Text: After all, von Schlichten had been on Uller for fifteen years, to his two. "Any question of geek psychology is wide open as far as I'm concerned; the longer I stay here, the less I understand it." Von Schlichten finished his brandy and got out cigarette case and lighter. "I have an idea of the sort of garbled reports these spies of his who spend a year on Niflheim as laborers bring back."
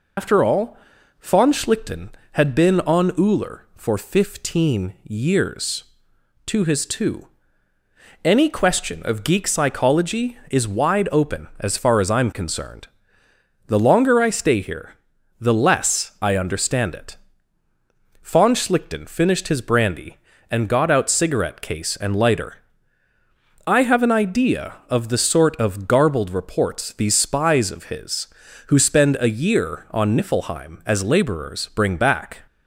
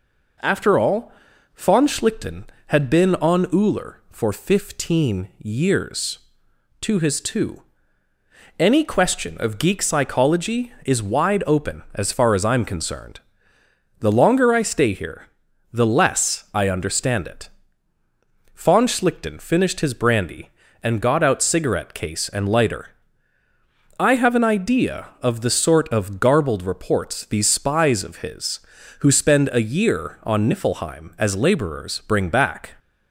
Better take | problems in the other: second | loses the start of "After"; at 0.1 s; 125 ms

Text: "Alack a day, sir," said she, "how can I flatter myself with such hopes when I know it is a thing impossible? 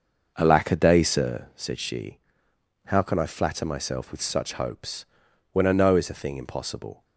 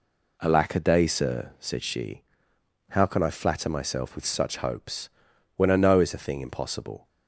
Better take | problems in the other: second | starts louder than the rest; noticeable; until 1.3 s; 6 dB // pauses between "hopes" and "when"; noticeable; at 5.0 s; 0.48 s long; noticeable in the second

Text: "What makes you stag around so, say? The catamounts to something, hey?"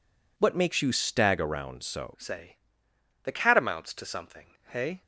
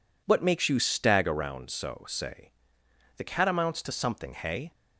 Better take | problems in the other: second | changes voice at "say"; from 2.1 s on; 2.9 s long

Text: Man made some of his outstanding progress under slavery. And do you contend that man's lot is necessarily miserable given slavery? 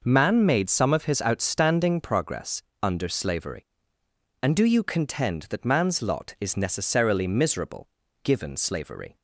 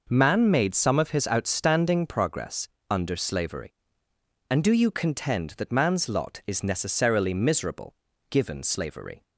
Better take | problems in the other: neither | pauses between "progress" and "under"; slight; the same in both // pauses between "miserable" and "given"; the same in both

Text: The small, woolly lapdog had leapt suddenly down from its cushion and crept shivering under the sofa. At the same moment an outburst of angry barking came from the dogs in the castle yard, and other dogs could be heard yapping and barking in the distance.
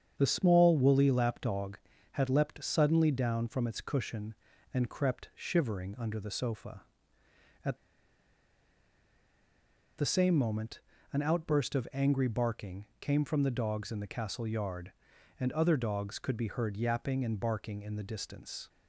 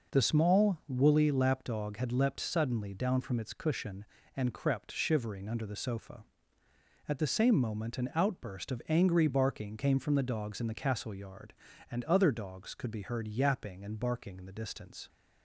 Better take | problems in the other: second | starts louder than the rest; strong; until 1.2 s; 7.5 dB // pauses between "At" and "the"; strong; at 7.7 s; 2.2 s long // pauses between "moment" and "an"; slight; at 10.8 s; 0.32 s long

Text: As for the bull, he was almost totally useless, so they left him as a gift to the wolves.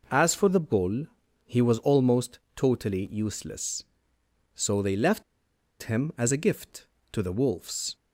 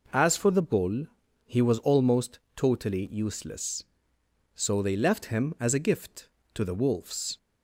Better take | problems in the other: second | pauses between "almost" and "totally"; slight; at 2.3 s; 0.18 s long; slight in the second // pauses between "left" and "him"; noticeable; at 5.2 s; 0.59 s long

